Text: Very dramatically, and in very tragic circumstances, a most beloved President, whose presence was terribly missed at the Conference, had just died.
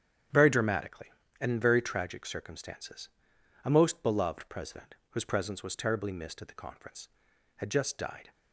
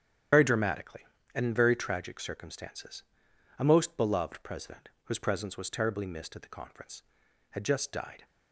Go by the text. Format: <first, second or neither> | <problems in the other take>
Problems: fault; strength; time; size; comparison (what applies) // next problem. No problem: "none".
first | loses the start of "Very"; at 0.3 s; 70 ms // starts louder than the rest; strong; until 1.6 s; 9.5 dB; strong in the first